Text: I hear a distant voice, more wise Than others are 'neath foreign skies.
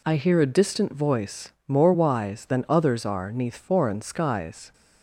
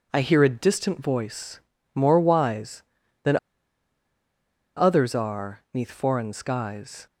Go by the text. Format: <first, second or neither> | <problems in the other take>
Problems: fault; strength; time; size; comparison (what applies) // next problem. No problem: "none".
first | pauses between "Than" and "others"; strong; at 3.3 s; 1.3 s long